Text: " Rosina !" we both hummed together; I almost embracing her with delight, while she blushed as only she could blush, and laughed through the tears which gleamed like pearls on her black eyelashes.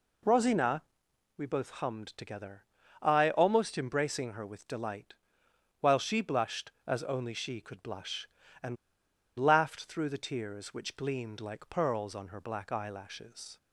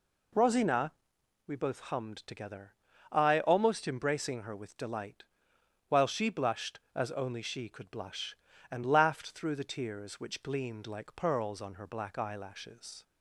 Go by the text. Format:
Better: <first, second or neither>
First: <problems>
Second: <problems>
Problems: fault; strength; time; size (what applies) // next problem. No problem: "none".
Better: second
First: pauses between "and" and "laughed"; noticeable; at 8.7 s; 0.62 s long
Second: none